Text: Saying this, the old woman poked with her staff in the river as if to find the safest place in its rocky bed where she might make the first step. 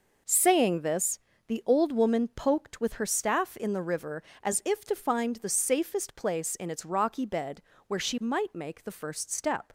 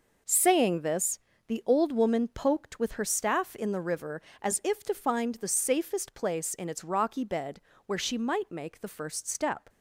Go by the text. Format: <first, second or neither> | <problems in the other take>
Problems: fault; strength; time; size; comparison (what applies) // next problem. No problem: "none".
neither | pauses between "bed" and "where"; slight; the same in both